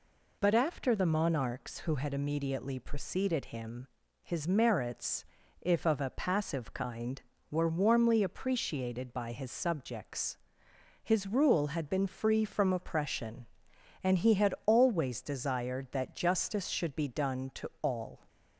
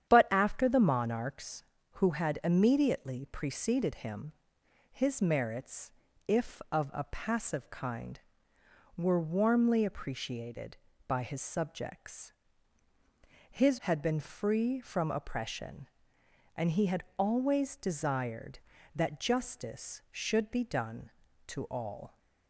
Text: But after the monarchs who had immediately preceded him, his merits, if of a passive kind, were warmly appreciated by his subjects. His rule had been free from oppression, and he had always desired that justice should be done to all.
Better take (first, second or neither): first